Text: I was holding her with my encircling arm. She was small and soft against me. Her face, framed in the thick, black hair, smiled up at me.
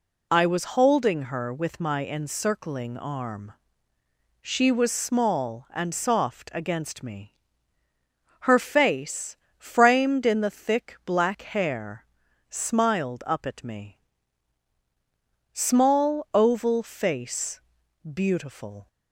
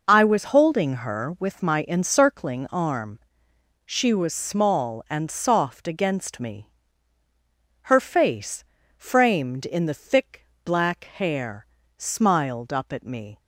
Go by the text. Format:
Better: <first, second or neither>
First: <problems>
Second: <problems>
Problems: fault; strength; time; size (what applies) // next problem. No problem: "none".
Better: second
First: goes on to say "Small oval face beautiful"; strong; from 15.5 s on; 3.3 s long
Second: none